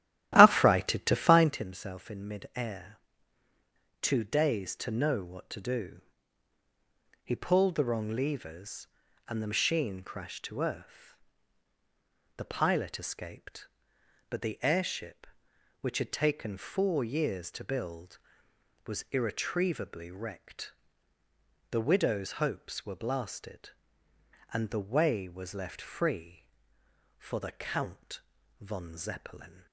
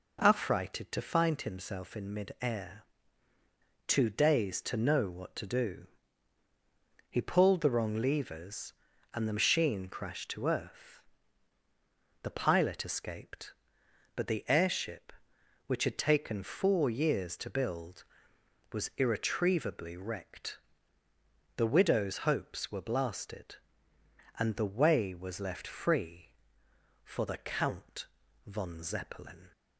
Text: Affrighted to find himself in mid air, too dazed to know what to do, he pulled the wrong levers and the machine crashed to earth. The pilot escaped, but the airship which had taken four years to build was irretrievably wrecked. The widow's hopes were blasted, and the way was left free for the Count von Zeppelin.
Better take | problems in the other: second | starts louder than the rest; strong; until 1.7 s; 13.5 dB // pauses between "Count" and "von"; at 28.1 s; 0.40 s long; also in the second

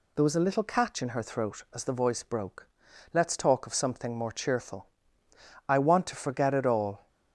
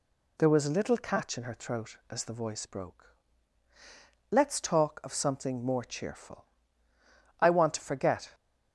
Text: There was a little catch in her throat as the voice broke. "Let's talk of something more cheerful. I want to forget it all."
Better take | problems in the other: first | stops before "it all"; at 8.3 s

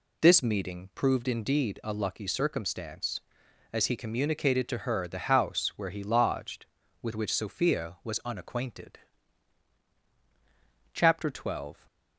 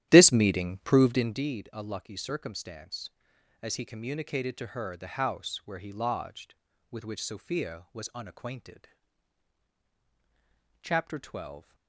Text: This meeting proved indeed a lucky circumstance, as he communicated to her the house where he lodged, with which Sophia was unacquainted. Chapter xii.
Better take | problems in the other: first | starts louder than the rest; strong; until 1.5 s; 12 dB

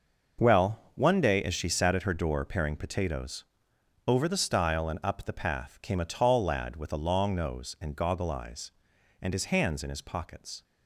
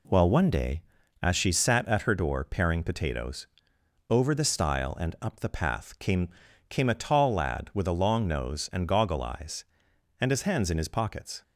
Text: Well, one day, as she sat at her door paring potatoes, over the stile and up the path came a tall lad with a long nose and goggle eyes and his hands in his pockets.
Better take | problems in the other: first | says "came" twice; at 6.6 s

